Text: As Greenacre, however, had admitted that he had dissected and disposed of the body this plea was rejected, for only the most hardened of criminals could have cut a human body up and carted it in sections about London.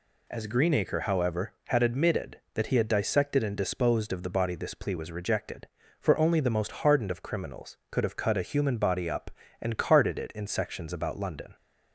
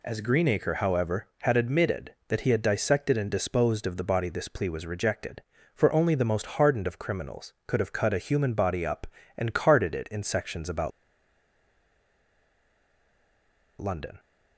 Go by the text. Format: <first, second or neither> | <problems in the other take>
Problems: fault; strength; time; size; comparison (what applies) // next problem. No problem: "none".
first | pauses between "about" and "London"; strong; at 10.9 s; 2.9 s long